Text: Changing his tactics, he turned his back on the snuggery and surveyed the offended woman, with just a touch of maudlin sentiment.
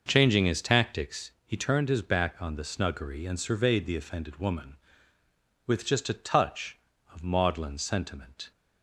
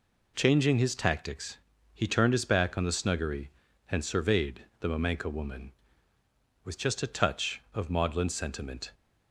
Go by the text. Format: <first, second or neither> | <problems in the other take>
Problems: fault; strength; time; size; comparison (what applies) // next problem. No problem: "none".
first | pauses between "surveyed" and "the"; slight; at 4.6 s; 0.16 s long // says "mamenka" for "offended"; at 4.8 s